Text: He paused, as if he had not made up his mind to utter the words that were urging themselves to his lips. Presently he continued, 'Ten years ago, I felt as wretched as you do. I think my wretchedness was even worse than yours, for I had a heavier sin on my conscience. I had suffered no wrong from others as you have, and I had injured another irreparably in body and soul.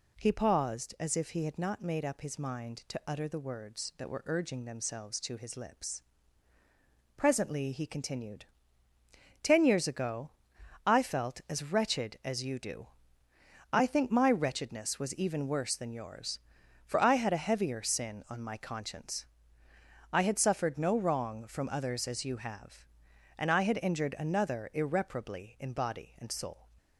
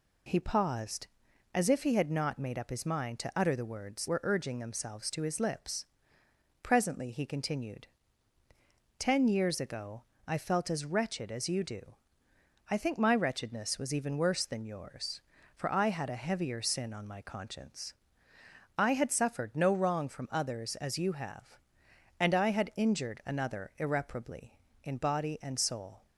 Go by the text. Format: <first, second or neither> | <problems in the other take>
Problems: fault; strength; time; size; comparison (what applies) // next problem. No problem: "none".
first | skips "that"; at 4.0 s